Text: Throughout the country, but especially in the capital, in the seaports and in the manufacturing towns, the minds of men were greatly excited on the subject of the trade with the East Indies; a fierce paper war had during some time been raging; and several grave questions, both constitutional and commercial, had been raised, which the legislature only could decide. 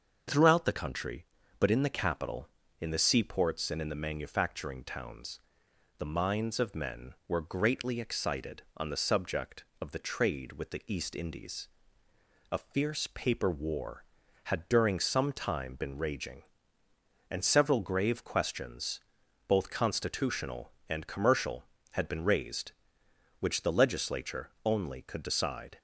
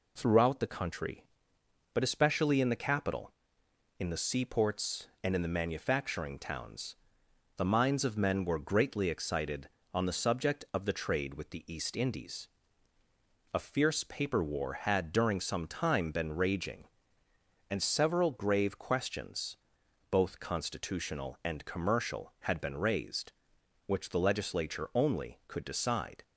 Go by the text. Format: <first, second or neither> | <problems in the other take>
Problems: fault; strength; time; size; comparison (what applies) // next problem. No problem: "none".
second | starts louder than the rest; until 1.6 s; 6.5 dB // skips "especially"; at 1.7 s